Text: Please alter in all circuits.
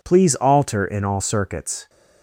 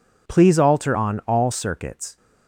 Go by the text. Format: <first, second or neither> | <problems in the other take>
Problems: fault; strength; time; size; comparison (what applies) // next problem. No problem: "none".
first | says "on" for "in"; at 0.9 s